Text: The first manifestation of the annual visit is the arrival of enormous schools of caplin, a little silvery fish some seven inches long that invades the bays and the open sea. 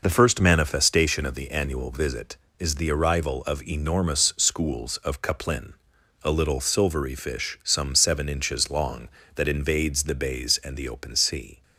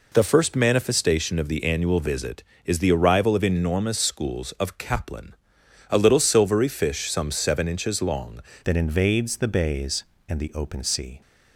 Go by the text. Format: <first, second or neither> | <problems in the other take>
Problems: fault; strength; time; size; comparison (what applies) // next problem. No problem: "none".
first | changes voice at "that"; from 8.6 s on; 2.6 s long